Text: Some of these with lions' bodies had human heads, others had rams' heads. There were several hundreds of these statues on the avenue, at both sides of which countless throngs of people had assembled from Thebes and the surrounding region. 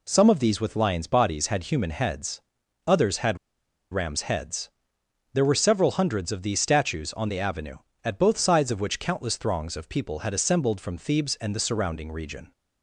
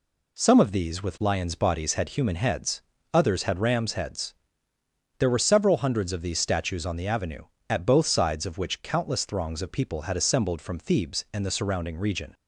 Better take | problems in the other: second | pauses between "had" and "rams"; noticeable; at 3.3 s; 0.54 s long

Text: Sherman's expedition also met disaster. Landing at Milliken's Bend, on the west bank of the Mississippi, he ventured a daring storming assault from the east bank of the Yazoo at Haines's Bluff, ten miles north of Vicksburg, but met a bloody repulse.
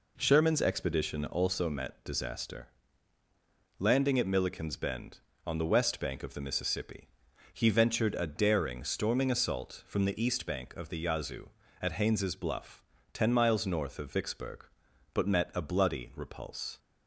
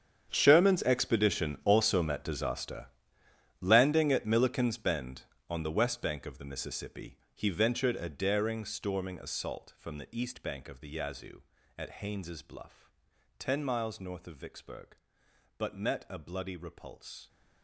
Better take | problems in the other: first | gets quieter; strong; throughout; 16.5 dB

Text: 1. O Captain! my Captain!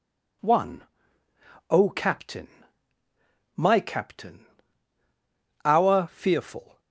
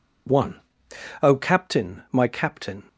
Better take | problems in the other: second | goes on to say "our fearful"; noticeable; from 5.6 s on; 1.1 s long

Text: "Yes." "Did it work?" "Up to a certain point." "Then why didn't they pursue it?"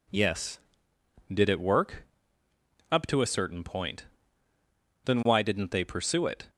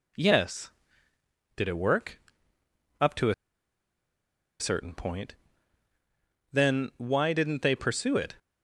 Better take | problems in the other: first | pauses between "a" and "certain"; strong; at 3.3 s; 1.2 s long

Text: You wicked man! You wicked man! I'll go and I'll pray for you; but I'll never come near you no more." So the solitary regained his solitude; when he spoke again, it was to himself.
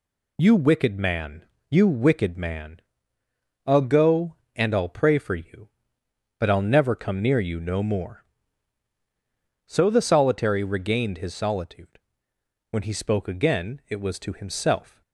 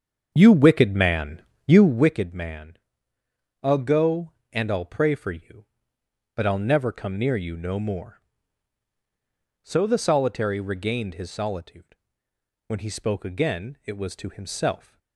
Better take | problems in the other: first | starts louder than the rest; strong; until 2.2 s; 7 dB

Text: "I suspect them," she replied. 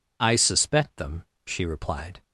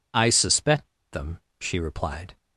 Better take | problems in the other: first | pauses between "suspect" and "them"; slight; at 0.8 s; 0.21 s long

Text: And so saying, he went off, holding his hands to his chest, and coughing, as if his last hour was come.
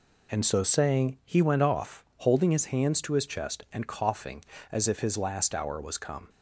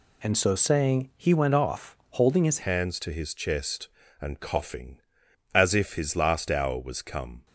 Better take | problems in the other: first | changes voice at "hands"; from 2.6 s on; 4.8 s long

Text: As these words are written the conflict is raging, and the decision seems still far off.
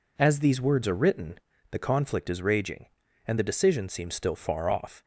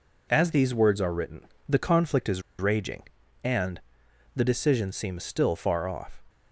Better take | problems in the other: first | pauses between "written" and "the"; slight; at 1.4 s; 0.24 s long; slight in the first // pauses between "is" and "raging"; slight; at 2.4 s; 0.18 s long // pauses between "and" and "the"; noticeable; at 3.7 s; 0.54 s long

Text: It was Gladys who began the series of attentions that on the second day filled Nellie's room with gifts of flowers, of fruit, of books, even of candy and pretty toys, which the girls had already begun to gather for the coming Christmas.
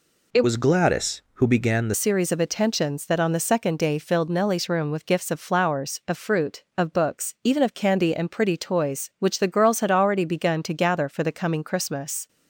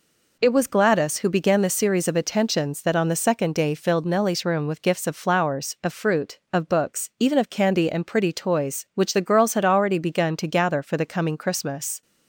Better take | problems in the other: second | changes voice from "was" to "the"; from 0.4 to 1.9 s; 1.5 s long

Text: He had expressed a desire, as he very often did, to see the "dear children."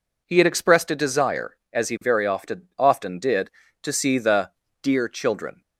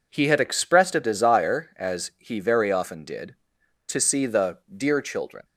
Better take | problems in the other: second | says "often" twice; at 2.7 s // pauses between "the" and "dear"; slight; at 4.5 s; 0.30 s long; slight in the second

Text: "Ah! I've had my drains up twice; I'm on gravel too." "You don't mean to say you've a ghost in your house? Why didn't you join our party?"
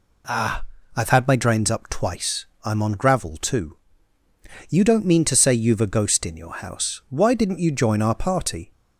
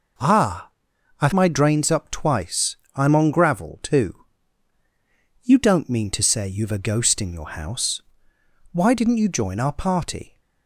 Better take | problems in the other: first | skips "had"; at 1.3 s

